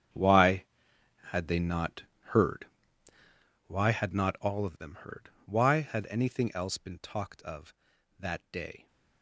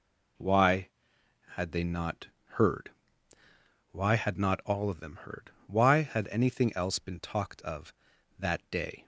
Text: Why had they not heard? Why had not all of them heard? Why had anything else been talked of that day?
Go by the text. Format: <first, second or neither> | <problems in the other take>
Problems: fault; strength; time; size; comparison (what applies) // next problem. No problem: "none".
second | gets quieter; strong; throughout; 14.5 dB // pauses between "not" and "heard"; slight; at 2.0 s; 0.26 s long; slight in the second